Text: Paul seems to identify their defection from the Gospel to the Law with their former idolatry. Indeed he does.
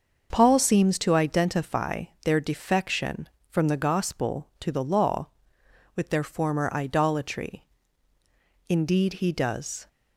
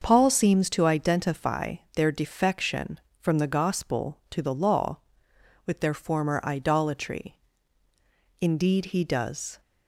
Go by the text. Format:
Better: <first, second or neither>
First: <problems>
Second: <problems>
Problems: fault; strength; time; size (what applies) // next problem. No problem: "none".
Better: neither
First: starts louder than the rest; until 1.3 s; 6.5 dB // pauses between "identify" and "their"; slight; at 2.0 s; 0.18 s long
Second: starts louder than the rest; until 1.0 s; 6.5 dB // pauses between "identify" and "their"; slight; at 1.7 s; 0.18 s long